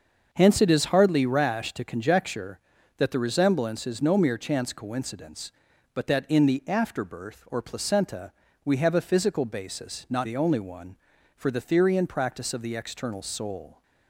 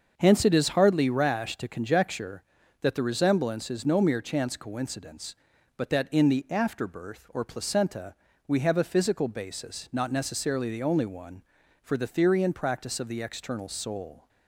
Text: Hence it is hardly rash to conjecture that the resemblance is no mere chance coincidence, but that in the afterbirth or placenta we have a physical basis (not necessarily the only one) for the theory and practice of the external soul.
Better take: second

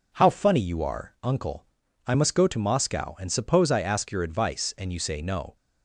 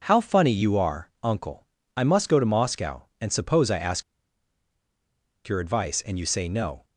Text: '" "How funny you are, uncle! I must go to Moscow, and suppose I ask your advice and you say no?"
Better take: first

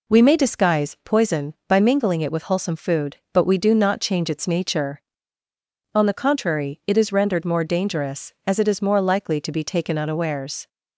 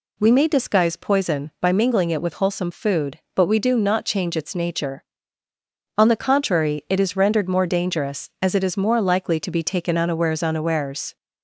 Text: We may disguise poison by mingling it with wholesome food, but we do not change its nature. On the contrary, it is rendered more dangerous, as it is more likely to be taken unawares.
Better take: first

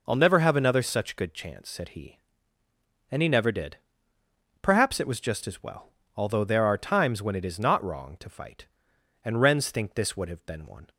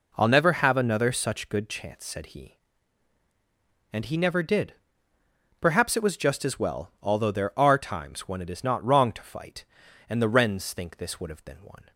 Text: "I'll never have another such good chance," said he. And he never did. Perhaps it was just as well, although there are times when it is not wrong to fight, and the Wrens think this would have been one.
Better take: second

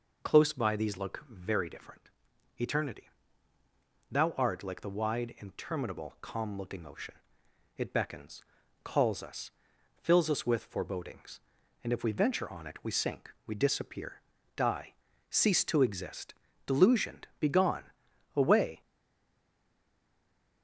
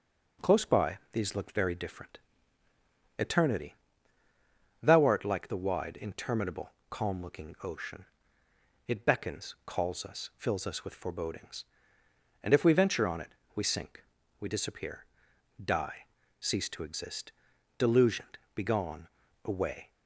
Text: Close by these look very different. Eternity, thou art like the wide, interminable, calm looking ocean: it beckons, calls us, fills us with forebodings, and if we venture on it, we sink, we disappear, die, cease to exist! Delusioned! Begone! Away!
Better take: second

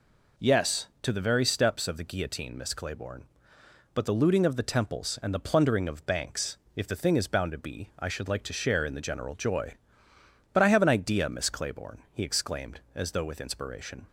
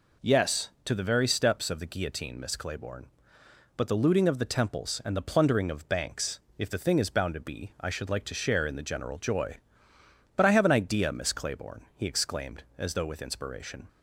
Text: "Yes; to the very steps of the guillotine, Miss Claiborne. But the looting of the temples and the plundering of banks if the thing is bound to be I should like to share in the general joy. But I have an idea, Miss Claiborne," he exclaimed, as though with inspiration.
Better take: neither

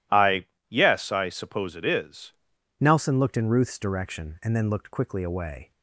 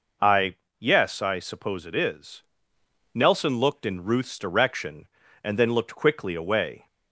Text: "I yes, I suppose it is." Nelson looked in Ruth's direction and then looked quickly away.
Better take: second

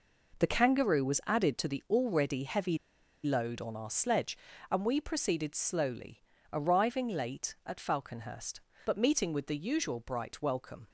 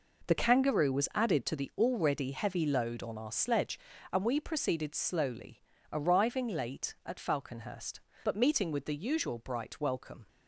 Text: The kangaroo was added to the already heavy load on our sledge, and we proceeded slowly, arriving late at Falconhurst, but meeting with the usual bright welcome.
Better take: second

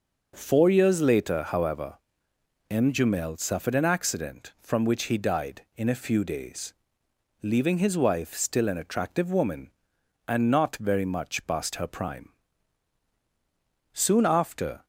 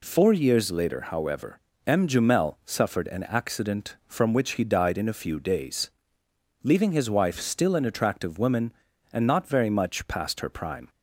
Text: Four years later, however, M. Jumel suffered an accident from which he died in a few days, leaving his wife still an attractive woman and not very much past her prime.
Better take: second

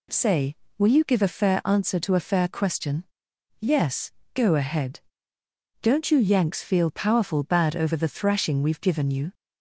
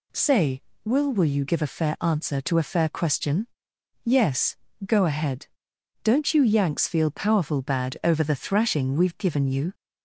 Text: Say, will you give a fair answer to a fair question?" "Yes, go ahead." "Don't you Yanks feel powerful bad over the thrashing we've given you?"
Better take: first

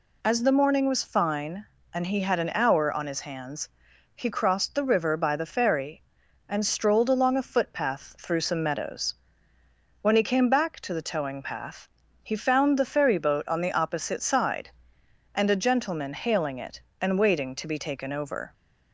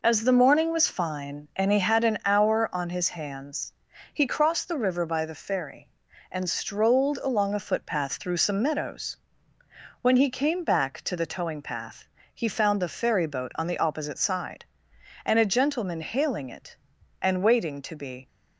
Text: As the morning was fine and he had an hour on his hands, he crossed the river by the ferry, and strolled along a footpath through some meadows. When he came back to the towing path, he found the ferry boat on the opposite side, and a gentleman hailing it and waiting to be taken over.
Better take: first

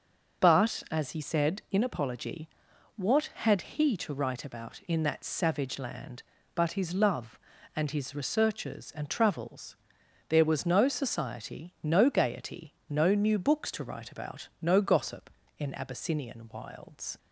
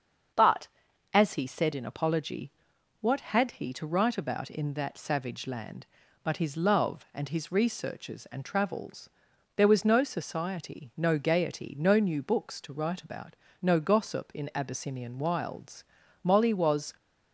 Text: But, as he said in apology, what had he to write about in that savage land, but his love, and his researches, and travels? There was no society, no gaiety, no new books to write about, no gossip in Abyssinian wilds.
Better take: first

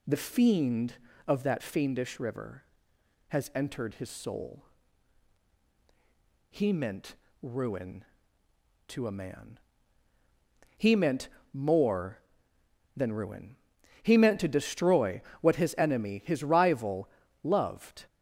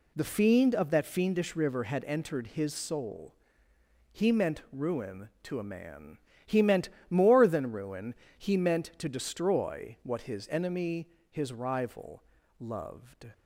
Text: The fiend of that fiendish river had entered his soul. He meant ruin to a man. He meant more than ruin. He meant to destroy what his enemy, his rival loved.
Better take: second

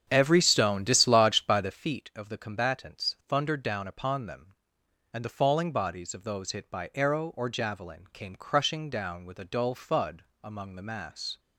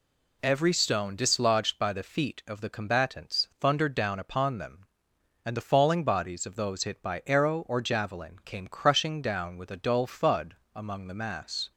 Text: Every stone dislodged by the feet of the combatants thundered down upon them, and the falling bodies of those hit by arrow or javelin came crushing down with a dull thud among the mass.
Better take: second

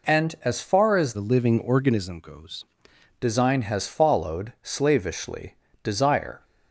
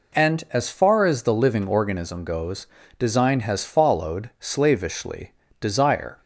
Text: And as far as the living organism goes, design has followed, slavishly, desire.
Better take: second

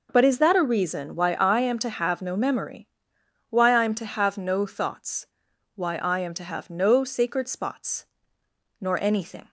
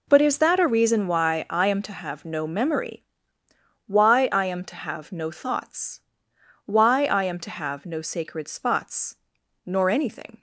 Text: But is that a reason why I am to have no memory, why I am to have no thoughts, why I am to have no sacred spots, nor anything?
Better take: neither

